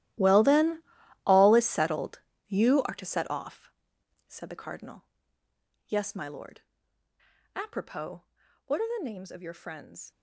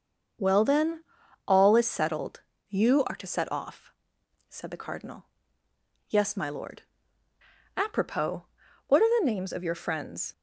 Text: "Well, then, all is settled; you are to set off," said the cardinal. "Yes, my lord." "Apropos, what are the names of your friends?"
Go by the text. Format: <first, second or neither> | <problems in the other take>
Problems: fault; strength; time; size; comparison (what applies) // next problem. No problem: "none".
second | gets quieter; strong; throughout; 15.5 dB // starts louder than the rest; strong; until 1.6 s; 14.5 dB; also in the second